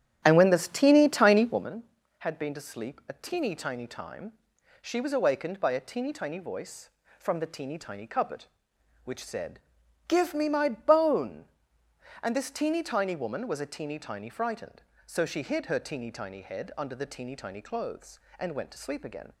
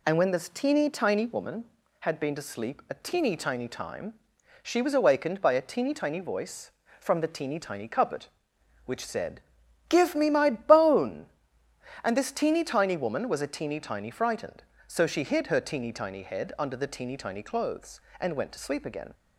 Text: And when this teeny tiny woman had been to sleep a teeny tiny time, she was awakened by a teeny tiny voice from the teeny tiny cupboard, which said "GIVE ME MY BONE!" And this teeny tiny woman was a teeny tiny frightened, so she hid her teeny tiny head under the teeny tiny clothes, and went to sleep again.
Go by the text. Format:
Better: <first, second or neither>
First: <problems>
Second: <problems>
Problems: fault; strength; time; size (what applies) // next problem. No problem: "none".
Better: second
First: starts louder than the rest; strong; until 1.7 s; 10.5 dB // pauses between "said" and "GIVE"; noticeable; at 9.5 s; 0.48 s long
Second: pauses between "said" and "GIVE"; noticeable; at 9.3 s; 0.48 s long